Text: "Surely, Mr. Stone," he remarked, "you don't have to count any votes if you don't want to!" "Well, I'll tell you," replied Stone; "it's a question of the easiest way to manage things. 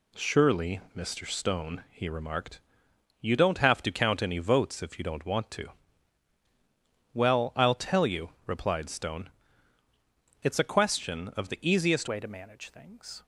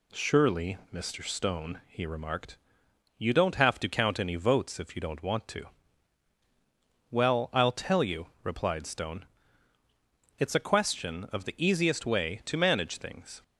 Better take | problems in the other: second | changes voice at "way"; from 12.0 s on; 1.2 s long

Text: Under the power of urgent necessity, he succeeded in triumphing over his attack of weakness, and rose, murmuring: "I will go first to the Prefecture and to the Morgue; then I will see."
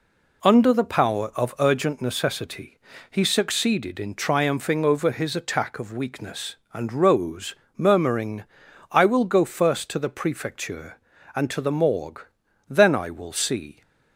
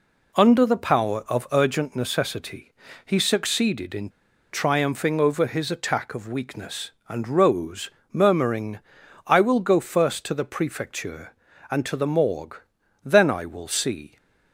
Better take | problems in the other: first | pauses between "in" and "triumphing"; at 4.0 s; 0.43 s long

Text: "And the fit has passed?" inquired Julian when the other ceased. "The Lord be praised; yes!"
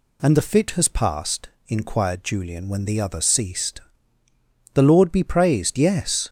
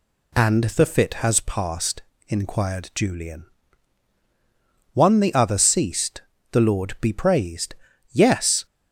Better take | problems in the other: first | says "one" for "when"; at 4.9 s

